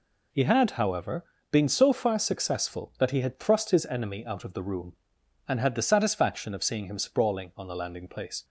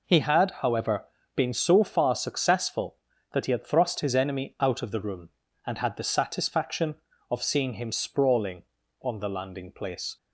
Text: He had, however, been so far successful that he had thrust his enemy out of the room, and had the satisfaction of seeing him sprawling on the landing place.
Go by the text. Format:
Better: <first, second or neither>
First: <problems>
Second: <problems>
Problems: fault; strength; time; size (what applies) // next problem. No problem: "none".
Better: neither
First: none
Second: none